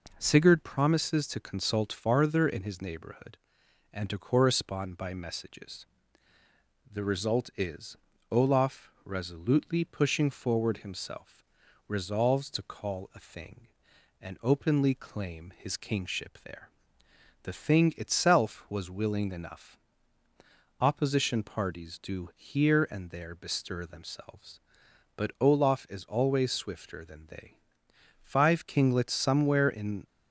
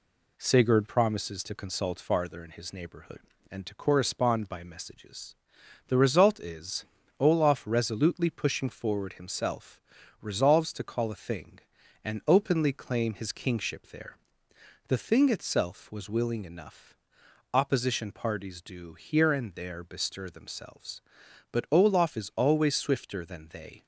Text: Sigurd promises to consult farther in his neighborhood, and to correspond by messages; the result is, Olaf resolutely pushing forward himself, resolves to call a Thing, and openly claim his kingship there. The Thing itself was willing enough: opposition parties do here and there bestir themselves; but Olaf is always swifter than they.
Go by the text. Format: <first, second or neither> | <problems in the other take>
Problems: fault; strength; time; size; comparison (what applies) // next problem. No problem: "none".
second | goes on to say "Five kinglets somewhere in"; strong; from 28.2 s on; 1.8 s long